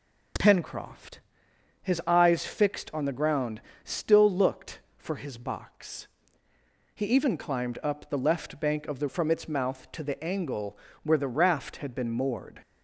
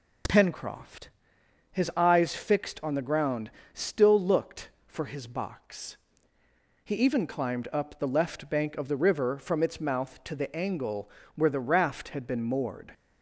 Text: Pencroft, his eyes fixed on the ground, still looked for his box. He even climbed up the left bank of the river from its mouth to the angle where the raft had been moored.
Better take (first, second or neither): second